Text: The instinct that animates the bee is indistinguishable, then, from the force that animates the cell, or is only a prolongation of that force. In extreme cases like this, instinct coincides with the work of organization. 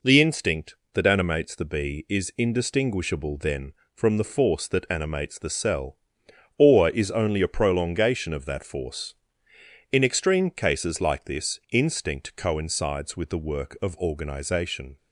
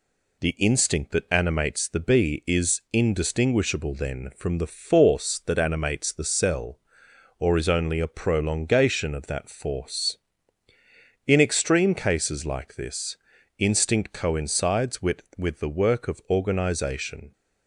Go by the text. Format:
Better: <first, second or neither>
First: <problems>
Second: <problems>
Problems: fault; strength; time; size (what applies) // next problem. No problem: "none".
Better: first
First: none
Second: says "with" twice; at 15.3 s